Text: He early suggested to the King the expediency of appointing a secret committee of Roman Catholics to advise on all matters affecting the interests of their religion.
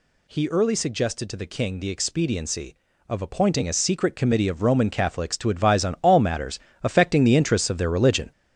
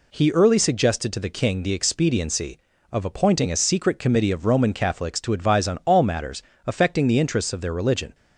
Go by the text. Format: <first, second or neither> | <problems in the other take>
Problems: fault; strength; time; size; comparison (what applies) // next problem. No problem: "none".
second | gets louder; throughout; 7 dB // pauses between "matters" and "affecting"; slight; at 6.5 s; 0.24 s long; slight in the second